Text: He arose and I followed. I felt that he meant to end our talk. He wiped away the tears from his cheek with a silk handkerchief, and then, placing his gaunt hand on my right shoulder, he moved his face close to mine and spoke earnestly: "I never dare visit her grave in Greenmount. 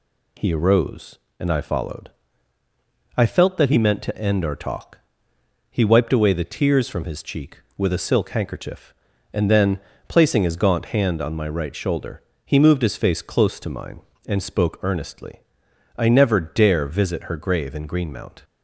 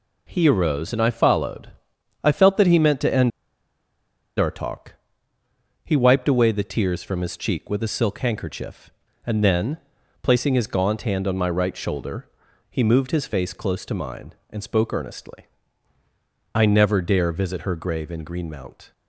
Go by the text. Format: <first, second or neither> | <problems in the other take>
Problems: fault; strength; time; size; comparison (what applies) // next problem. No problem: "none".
first | pauses between "end" and "our"; at 3.3 s; 1.0 s long